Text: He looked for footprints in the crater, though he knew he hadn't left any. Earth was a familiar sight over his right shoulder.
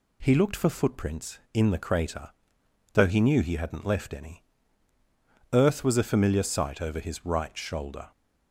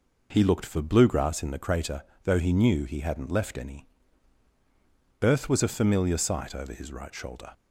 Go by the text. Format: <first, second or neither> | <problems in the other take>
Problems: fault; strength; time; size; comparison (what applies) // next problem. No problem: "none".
first | says "bluegrass" for "footprints"; at 0.8 s